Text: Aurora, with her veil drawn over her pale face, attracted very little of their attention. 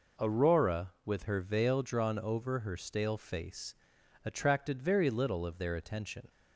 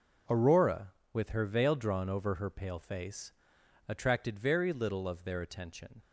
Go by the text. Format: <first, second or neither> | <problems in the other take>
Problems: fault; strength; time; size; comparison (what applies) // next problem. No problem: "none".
second | says "stale" for "pale"; at 2.7 s